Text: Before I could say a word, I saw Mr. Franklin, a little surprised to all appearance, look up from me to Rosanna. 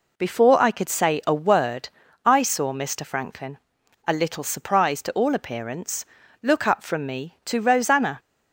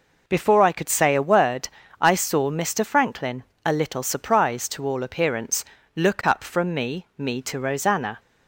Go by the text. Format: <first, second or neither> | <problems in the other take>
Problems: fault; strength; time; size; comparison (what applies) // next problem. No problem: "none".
first | says "me" twice; at 7.1 s